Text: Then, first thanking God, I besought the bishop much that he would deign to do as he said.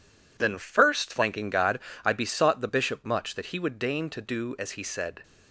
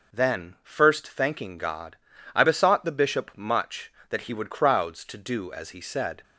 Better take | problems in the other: first | says "crowds" for "deign"; at 4.4 s

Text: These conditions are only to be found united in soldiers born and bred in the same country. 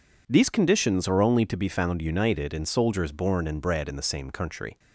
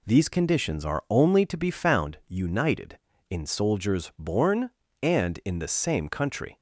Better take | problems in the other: first | skips "bred"; at 5.4 s

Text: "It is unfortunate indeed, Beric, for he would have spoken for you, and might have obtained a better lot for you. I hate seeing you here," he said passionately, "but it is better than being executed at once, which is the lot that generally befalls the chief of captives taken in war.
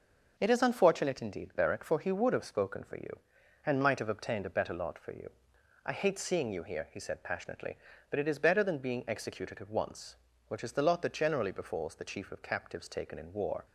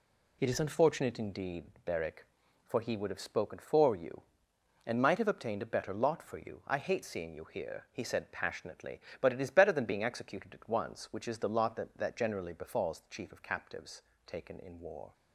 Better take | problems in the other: first | says "that" twice; at 11.9 s // pauses between "captives" and "taken"; slight; at 14.0 s; 0.24 s long

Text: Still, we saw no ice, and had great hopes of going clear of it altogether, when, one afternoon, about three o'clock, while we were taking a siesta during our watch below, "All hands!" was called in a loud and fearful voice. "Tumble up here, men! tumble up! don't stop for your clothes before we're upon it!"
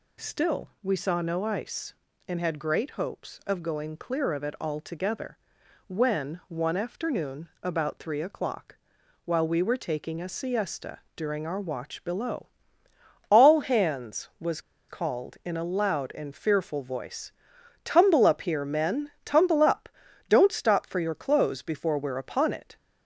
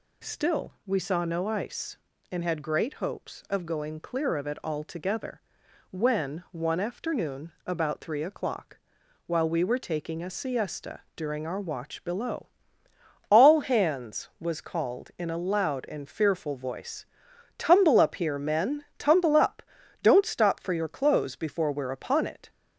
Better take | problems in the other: second | pauses between "siesta" and "during"; slight; at 10.9 s; 0.16 s long // pauses between "was" and "called"; slight; at 14.5 s; 0.29 s long

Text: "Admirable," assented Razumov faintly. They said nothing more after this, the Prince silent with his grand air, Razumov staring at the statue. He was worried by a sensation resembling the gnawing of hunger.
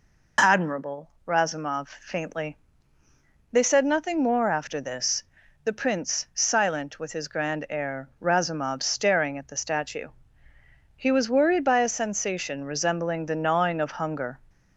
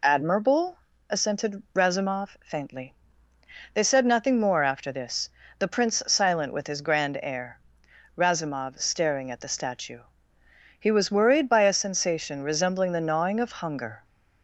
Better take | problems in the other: second | skips "assented"; at 1.1 s

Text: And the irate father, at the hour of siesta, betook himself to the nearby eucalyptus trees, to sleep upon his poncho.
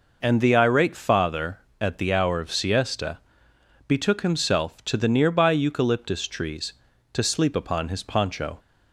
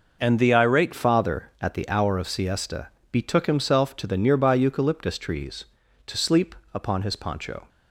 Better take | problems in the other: first | changes voice at "father"; from 0.9 s on; 6.7 s long // pauses between "sleep" and "upon"; slight; at 6.5 s; 0.18 s long

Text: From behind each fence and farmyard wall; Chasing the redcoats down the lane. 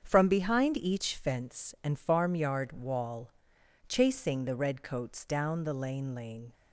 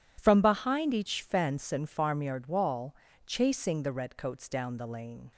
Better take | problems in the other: second | starts louder than the rest; strong; until 1.0 s; 7.5 dB // says "lane" twice; at 6.1 s

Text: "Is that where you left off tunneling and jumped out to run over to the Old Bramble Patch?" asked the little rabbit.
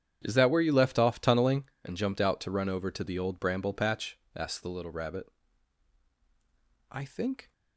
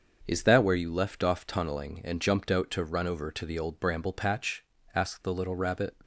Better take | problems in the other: second | starts louder than the rest; strong; until 1.2 s; 8.5 dB; also in the second // goes on to say "I think"; from 6.9 s on; 0.60 s long

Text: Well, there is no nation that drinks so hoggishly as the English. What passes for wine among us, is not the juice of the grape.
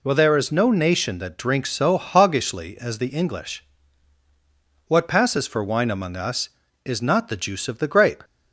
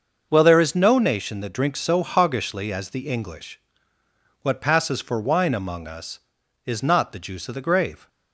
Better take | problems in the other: first | starts louder than the rest; until 1.3 s; 6 dB // says "grave" for "grape"; at 7.5 s

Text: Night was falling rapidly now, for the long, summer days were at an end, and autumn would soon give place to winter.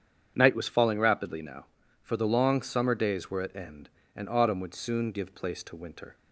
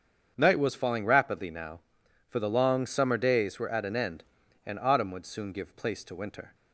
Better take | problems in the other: second | starts louder than the rest; strong; until 1.3 s; 8.5 dB; strong in the second // skips "an"; at 3.5 s

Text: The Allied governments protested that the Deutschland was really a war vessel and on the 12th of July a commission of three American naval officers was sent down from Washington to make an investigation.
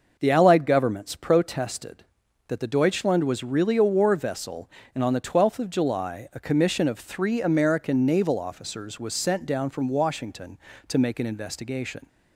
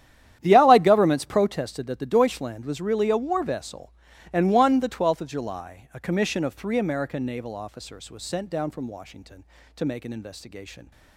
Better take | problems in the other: first | starts louder than the rest; strong; until 1.4 s; 10.5 dB // says "one" for "on"; at 4.5 s

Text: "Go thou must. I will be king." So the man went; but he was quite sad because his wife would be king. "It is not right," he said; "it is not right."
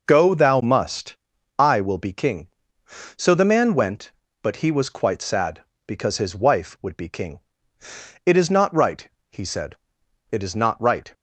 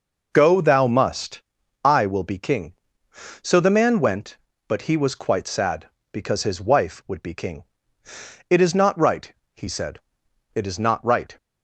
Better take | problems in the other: neither | none

